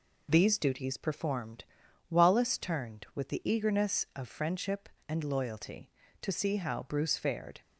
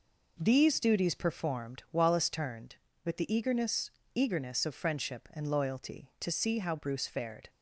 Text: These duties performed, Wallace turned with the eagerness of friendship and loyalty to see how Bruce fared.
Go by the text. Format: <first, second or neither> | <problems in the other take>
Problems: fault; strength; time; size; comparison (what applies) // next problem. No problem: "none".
first | says "eagerness" twice; at 4.1 s